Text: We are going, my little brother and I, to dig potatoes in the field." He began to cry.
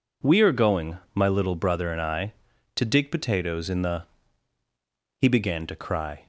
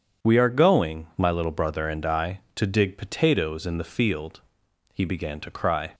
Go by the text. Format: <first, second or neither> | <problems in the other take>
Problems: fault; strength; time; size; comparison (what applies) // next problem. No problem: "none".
second | skips "field"; at 4.6 s